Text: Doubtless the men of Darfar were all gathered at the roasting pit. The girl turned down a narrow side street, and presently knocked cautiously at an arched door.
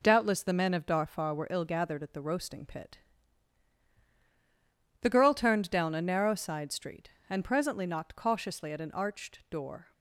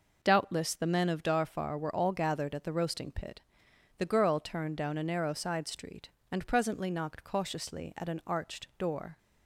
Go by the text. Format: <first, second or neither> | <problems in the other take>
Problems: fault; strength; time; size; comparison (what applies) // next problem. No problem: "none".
second | says "ill" for "all"; at 1.4 s